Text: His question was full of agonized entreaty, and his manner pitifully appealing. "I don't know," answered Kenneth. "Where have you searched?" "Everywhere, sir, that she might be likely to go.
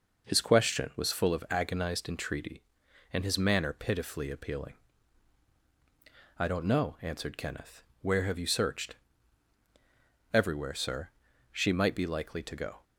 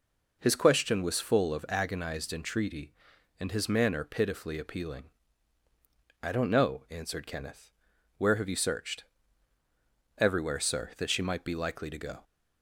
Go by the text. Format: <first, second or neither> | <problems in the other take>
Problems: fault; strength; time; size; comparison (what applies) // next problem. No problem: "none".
second | skips "that"; at 11.3 s